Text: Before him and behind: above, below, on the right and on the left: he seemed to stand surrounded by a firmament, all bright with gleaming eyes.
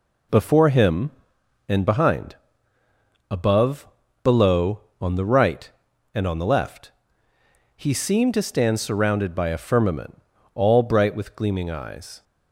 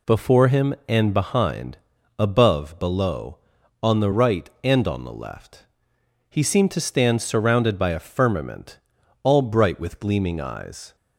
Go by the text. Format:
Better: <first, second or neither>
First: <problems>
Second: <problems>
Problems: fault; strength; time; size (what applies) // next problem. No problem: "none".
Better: neither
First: none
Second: none